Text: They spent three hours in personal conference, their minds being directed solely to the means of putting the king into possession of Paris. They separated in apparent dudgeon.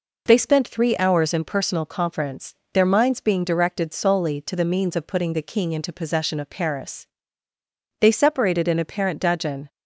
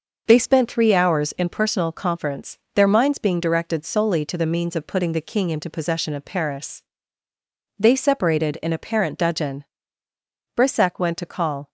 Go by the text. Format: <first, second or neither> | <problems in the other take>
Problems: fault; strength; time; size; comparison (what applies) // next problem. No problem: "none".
first | goes on to say "Brissac went to call"; noticeable; from 10.5 s on; 1.1 s long